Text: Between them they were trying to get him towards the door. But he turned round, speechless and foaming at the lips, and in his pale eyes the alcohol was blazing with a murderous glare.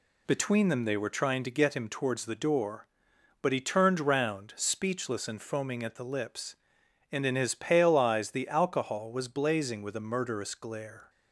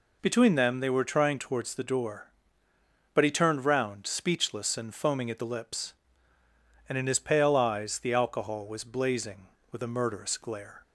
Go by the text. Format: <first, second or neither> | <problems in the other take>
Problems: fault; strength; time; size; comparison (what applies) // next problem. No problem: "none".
first | skips "to get him"; at 1.3 s